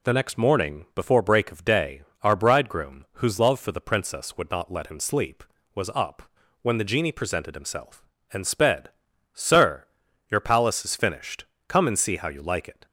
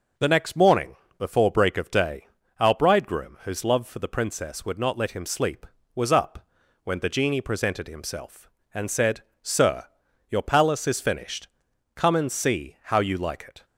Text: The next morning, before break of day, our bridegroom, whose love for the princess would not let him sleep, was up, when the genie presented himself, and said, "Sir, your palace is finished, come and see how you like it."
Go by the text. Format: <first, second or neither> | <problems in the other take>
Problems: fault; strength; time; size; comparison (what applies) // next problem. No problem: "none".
second | says "sped" for "said"; at 8.4 s